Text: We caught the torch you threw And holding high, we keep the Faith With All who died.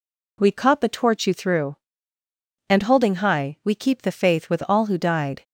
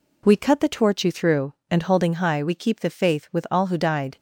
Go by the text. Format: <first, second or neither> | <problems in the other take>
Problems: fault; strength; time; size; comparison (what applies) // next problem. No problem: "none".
first | says "cut" for "caught"; at 0.3 s